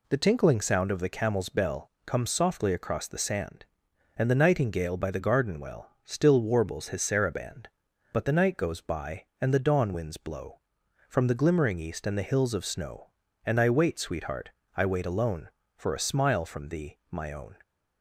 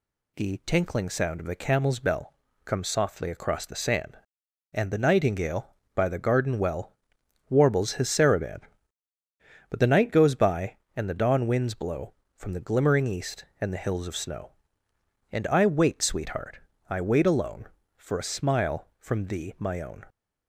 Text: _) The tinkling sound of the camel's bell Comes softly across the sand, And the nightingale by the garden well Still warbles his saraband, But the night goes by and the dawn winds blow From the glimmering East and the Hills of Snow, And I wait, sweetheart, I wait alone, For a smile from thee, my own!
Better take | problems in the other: first | pauses between "bell" and "Comes"; slight; at 2.3 s; 0.30 s long; slight in the first // skips "Still"; at 7.1 s

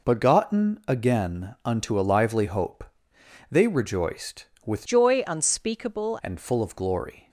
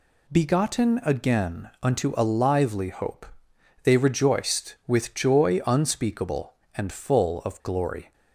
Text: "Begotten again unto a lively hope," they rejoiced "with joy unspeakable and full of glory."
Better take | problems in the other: second | changes voice from "joy" to "unspeakable"; from 4.8 to 6.1 s; 1.3 s long

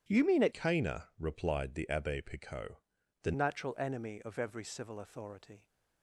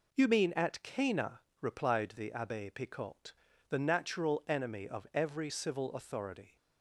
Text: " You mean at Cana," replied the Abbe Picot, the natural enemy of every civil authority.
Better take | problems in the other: second | starts louder than the rest; strong; until 1.0 s; 9.5 dB // changes voice from "Cana" to "the"; from 0.5 to 3.3 s; 2.8 s long

